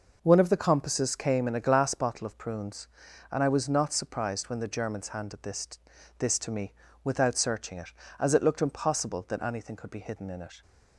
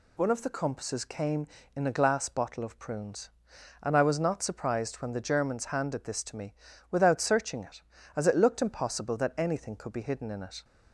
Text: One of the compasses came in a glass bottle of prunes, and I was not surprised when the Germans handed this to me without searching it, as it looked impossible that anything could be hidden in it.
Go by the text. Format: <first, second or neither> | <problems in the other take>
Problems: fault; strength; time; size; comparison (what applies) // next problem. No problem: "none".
second | says "this" twice; at 6.1 s // pauses between "me" and "without"; slight; at 6.7 s; 0.32 s long; slight in the second